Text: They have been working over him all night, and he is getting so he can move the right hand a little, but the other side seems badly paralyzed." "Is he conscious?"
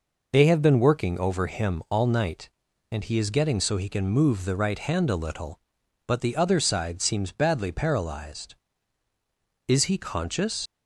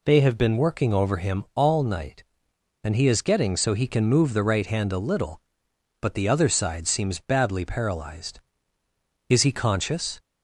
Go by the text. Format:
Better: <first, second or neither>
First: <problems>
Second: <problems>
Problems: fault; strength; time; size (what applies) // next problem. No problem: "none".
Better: second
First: leaves "conscious" unfinished; at 10.6 s; 65 ms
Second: none